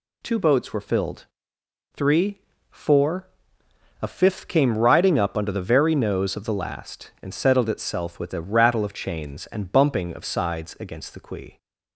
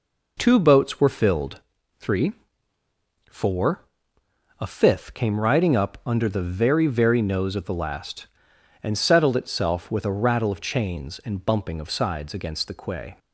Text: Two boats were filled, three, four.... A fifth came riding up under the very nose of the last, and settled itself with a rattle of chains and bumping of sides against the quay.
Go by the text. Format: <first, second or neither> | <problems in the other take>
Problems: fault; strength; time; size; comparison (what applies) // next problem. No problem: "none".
first | says "very" twice; at 6.8 s